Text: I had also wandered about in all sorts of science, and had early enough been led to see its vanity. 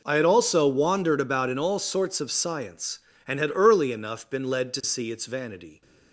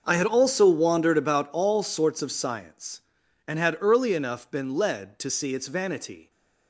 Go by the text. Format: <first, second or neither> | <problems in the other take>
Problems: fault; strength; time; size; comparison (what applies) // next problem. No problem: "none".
first | skips "in"; at 1.4 s